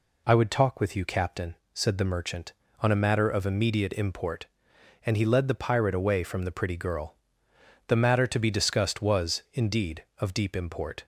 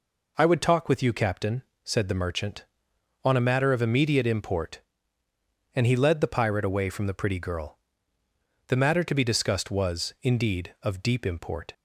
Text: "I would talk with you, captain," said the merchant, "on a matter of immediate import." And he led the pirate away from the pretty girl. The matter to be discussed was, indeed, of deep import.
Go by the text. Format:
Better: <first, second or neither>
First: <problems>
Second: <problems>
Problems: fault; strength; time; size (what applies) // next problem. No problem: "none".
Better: neither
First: none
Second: none